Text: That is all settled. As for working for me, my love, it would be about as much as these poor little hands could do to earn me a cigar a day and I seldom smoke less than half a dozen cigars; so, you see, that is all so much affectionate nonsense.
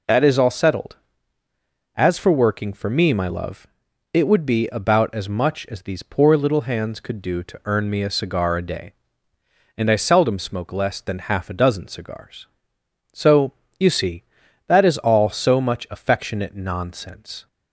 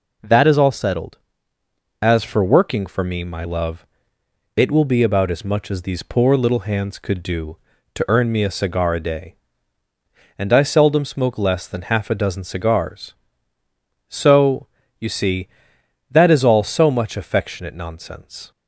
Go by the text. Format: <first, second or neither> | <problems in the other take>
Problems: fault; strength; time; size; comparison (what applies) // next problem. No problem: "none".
first | says "will" for "would"; at 4.7 s